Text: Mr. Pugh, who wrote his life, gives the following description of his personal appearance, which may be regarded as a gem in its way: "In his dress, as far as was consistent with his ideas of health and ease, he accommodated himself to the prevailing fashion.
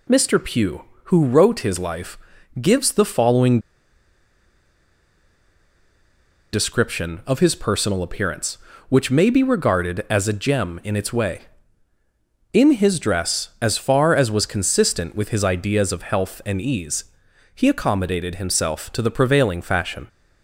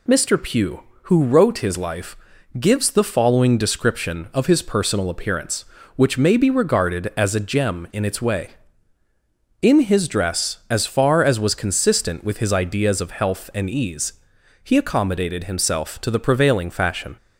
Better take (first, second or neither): second